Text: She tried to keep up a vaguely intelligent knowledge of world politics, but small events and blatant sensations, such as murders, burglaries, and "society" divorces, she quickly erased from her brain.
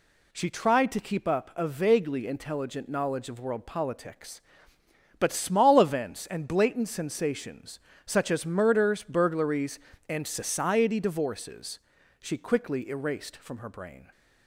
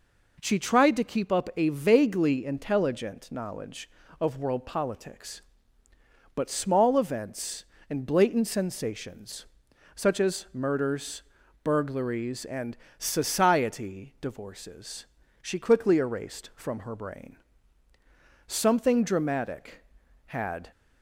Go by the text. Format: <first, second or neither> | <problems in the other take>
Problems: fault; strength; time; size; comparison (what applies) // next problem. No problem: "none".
first | pauses between "and" and "society"; slight; at 12.7 s; 0.22 s long // goes on to say "Something dramatic had"; strong; from 18.4 s on; 2.2 s long